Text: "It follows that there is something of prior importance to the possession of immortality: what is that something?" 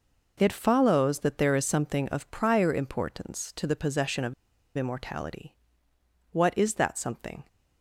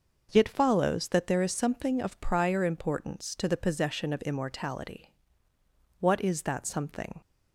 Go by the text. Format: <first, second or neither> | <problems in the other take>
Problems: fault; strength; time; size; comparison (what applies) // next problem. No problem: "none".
second | pauses between "of" and "immortality"; at 4.3 s; 0.44 s long